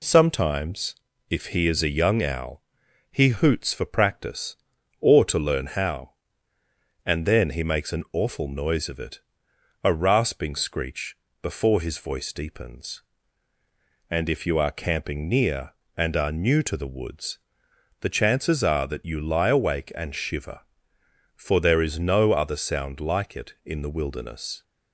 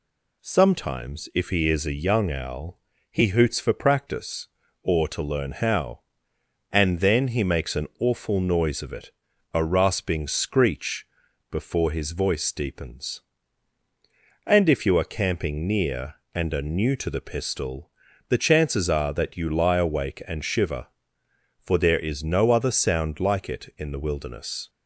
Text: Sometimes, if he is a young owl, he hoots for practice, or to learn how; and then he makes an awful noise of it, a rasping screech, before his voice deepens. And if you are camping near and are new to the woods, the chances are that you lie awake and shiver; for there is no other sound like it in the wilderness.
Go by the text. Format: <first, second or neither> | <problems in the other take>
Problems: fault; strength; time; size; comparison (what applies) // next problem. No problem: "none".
first | says "pistol" for "woods"; at 17.2 s